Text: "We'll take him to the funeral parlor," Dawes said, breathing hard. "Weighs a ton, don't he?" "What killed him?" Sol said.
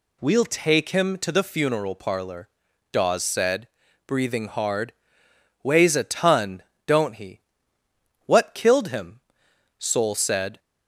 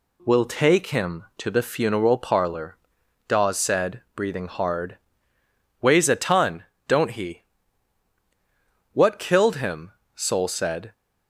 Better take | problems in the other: neither | none

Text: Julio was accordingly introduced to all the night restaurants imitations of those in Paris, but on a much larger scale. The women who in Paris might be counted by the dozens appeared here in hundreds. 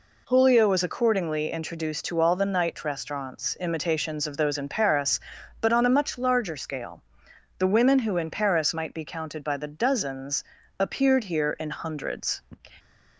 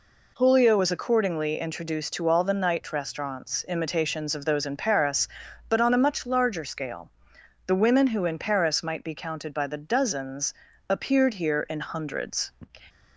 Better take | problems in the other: neither | pauses between "dozens" and "appeared"; slight; the same in both

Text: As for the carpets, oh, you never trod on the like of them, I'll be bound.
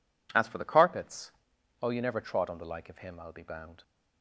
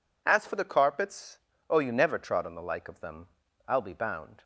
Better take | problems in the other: second | says "him" for "them"; at 2.9 s

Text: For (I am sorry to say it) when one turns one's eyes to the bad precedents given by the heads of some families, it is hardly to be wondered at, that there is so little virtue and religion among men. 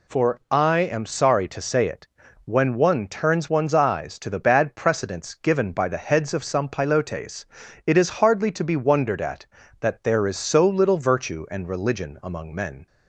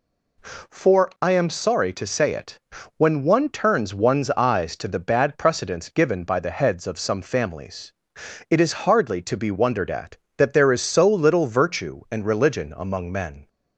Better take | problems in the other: second | says "pilotes" for "families"; at 6.7 s

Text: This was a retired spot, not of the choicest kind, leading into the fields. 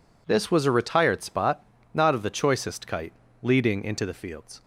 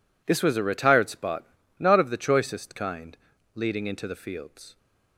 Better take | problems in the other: second | says "kite" for "kind"; at 2.8 s

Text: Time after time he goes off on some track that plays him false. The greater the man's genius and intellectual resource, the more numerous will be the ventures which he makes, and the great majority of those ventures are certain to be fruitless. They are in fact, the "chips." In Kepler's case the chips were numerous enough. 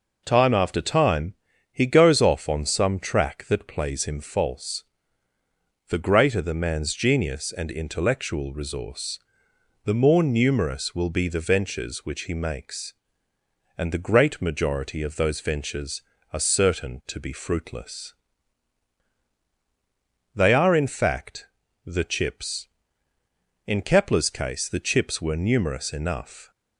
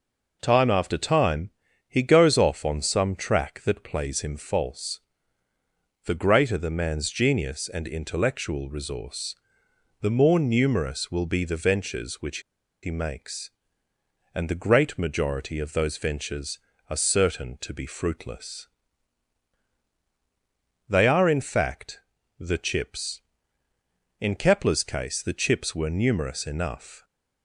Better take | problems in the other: first | pauses between "time" and "he"; at 1.4 s; 0.38 s long; also in the first // pauses between "which" and "he"; at 12.3 s; 0.43 s long

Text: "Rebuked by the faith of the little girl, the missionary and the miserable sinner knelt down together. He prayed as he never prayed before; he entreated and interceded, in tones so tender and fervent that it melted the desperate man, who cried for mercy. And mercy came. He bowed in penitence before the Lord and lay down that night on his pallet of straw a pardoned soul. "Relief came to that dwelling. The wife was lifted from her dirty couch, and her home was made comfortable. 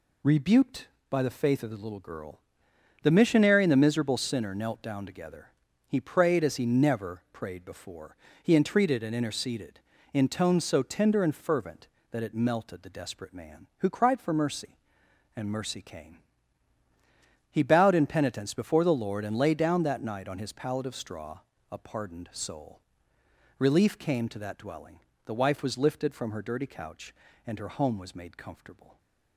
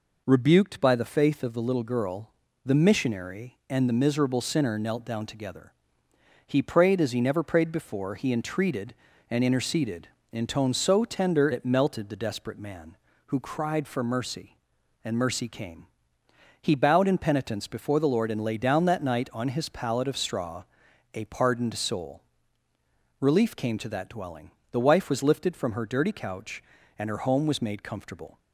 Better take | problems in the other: first | skips "and fervent that"; at 11.5 s // pauses between "straw" and "a"; noticeable; at 20.6 s; 0.50 s long; slight in the first

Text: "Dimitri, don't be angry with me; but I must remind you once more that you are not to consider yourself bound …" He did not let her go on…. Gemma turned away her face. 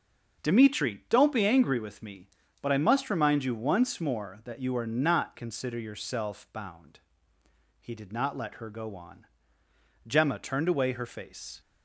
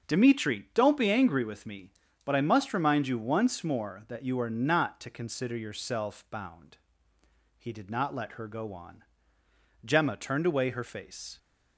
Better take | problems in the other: second | starts louder than the rest; strong; until 1.4 s; 8.5 dB; strong in the second // skips "to"; at 5.3 s

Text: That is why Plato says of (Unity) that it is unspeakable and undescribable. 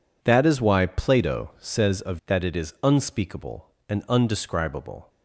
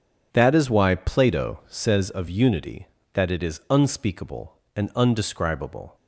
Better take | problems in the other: second | skips "Unity"; at 2.2 s

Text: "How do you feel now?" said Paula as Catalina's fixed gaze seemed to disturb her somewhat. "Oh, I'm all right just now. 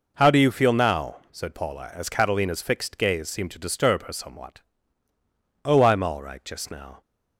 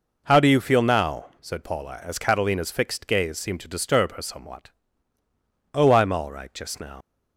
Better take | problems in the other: first | leaves "now" unfinished; at 7.0 s; 100 ms

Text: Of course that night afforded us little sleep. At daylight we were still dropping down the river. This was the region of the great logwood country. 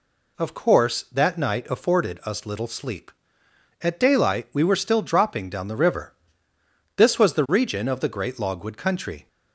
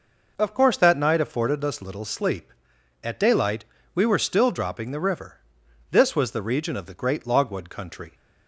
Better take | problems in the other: first | pauses between "daylight" and "we"; slight; at 3.6 s; 0.30 s long // skips "down"; at 4.9 s

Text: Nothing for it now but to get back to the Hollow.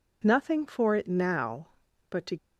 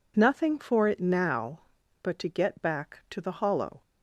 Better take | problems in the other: second | stops before "get back to the Hollow"; at 2.3 s

